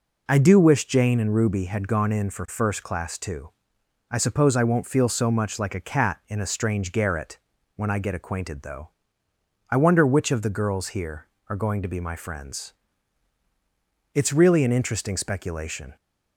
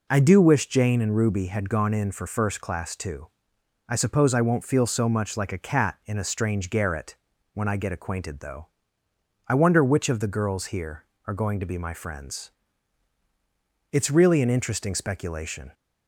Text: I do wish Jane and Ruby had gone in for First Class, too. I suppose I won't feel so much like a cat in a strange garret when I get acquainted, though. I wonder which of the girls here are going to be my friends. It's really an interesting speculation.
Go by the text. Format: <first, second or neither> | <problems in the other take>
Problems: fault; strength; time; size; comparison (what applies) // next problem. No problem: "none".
neither | pauses between "garret" and "when"; the same in both